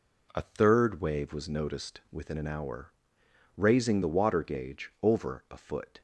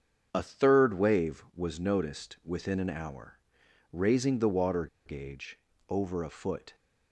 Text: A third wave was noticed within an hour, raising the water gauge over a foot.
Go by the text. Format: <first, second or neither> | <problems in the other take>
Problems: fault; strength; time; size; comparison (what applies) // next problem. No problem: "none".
first | starts louder than the rest; until 1.3 s; 7 dB // pauses between "water" and "gauge"; slight; at 4.8 s; 0.19 s long // pauses between "gauge" and "over"; slight; at 5.5 s; 0.30 s long